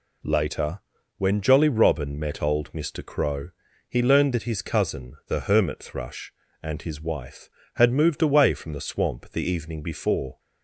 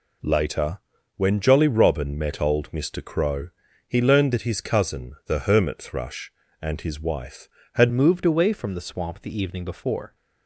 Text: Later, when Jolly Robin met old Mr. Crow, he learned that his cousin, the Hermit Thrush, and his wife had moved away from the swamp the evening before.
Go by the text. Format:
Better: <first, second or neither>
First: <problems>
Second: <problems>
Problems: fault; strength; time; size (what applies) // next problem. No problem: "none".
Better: first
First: none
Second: changes voice at "moved"; from 7.9 s on; 2.2 s long